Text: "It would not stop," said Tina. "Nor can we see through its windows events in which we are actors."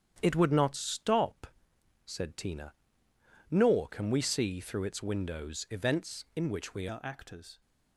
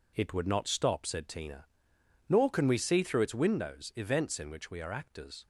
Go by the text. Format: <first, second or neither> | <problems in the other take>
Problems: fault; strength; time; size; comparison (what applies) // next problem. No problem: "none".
second | starts louder than the rest; strong; until 1.2 s; 9 dB // changes voice at "are"; from 6.8 s on; 0.8 s long